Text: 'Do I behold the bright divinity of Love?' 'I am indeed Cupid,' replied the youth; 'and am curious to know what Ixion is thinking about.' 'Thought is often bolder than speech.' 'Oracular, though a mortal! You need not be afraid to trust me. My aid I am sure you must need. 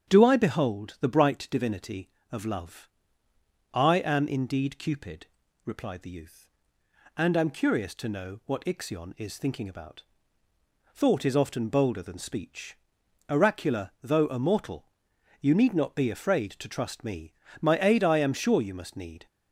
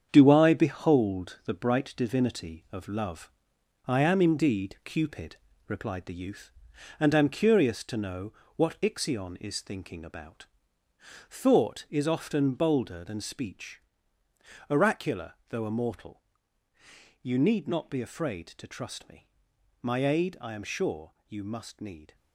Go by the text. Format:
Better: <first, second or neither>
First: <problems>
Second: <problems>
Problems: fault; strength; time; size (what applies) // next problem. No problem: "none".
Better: first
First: starts louder than the rest; strong; until 1.1 s; 8.5 dB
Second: gets quieter; strong; throughout; 8 dB // starts louder than the rest; strong; until 1.1 s; 8 dB // pauses between "know" and "what"; slight; at 8.3 s; 0.24 s long